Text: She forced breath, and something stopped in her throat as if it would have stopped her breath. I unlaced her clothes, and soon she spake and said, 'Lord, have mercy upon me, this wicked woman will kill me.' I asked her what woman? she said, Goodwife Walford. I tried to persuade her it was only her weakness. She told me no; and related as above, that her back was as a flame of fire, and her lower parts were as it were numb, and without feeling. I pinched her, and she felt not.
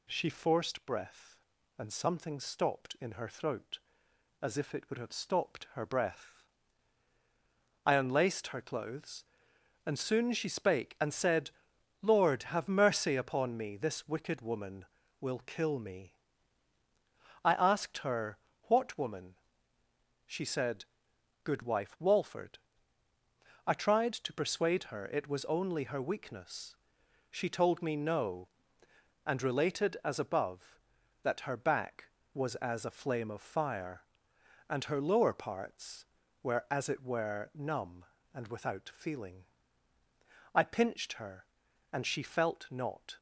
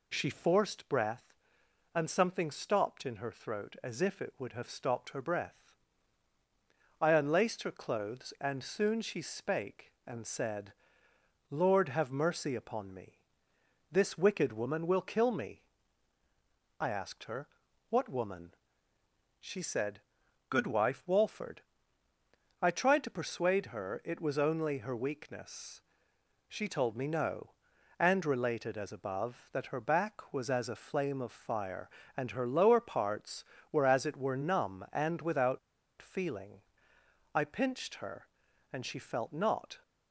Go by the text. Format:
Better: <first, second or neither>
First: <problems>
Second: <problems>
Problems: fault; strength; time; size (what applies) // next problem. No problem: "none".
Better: first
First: pauses between "her" and "what"; slight; at 18.3 s; 0.24 s long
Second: pauses between "her" and "what"; at 17.4 s; 0.40 s long // pauses between "without" and "feeling"; at 35.5 s; 0.42 s long